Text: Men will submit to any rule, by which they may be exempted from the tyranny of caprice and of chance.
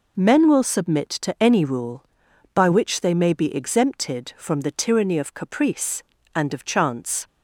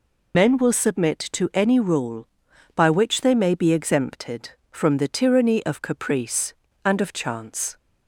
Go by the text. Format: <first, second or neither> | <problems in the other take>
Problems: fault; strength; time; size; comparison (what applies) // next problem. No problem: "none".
first | loses the start of "Men"; at 0.3 s; 75 ms